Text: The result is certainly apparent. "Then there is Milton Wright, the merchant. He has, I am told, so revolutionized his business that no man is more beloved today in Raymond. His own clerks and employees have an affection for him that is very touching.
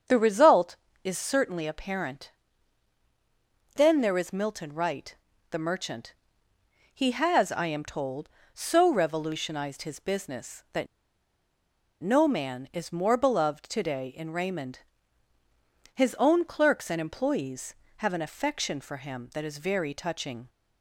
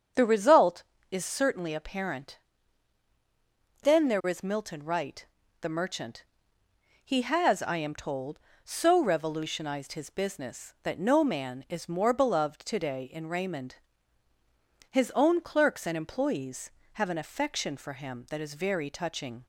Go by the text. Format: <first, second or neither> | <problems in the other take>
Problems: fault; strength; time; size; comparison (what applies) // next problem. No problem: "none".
second | starts louder than the rest; until 1.3 s; 7 dB; also in the second // pauses between "that" and "no"; at 10.8 s; 1.1 s long